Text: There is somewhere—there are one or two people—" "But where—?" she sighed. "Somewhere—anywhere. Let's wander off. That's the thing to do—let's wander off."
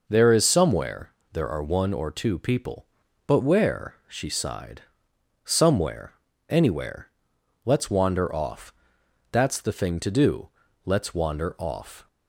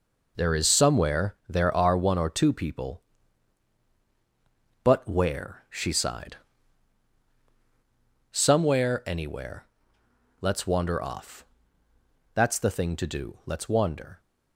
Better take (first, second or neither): first